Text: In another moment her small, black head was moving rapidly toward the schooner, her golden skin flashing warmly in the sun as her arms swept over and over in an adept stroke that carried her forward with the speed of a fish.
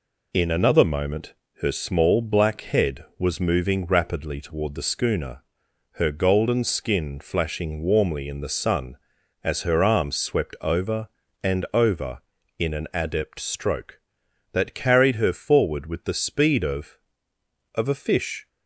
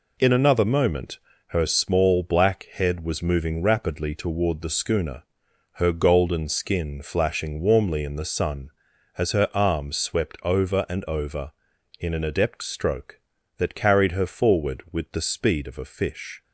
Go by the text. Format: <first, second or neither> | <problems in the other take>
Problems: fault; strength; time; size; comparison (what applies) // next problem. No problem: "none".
second | pauses between "moment" and "her"; slight; at 1.3 s; 0.28 s long; slight in the second // says "of" twice; at 17.7 s